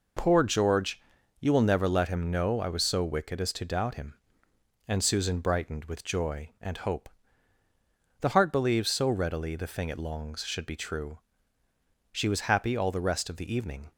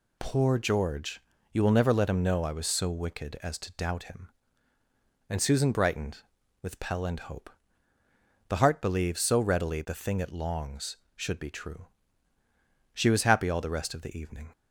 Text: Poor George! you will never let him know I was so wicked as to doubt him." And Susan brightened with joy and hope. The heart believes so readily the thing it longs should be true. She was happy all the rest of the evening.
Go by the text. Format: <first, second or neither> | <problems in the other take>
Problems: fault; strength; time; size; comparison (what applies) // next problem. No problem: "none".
first | says "pell" for "joy"; at 6.7 s